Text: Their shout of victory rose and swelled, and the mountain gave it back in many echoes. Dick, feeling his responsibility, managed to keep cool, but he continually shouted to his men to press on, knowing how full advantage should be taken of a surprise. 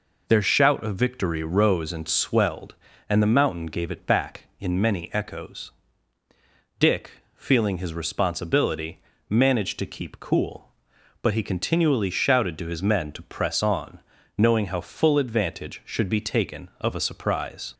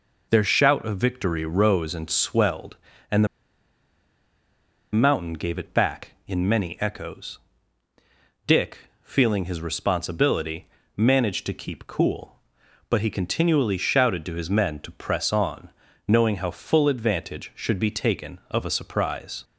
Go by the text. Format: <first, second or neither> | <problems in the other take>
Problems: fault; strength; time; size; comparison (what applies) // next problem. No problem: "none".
first | pauses between "and" and "the"; strong; at 3.2 s; 1.6 s long